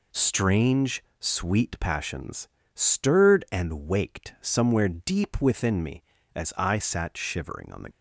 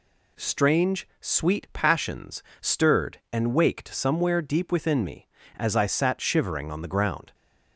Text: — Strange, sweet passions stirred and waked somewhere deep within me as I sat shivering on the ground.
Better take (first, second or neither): second